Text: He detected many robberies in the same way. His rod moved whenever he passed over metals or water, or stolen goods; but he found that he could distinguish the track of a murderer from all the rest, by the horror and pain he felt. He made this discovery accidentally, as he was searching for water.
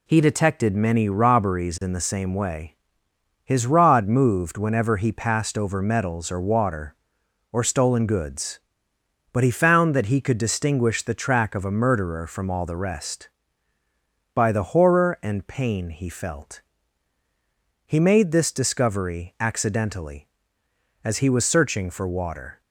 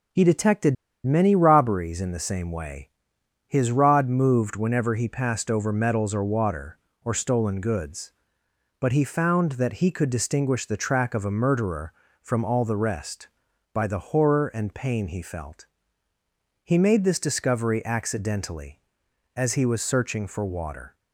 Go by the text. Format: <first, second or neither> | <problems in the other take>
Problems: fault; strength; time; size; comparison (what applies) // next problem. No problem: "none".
first | pauses between "detected" and "many"; slight; at 0.7 s; 0.29 s long